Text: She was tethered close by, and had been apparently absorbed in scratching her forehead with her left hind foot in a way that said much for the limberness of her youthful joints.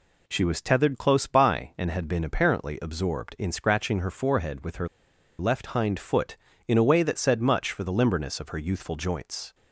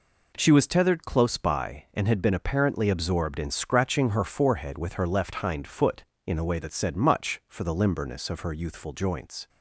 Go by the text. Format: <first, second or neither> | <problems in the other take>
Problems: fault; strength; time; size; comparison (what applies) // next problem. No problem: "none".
second | pauses between "her" and "left"; noticeable; at 4.8 s; 0.52 s long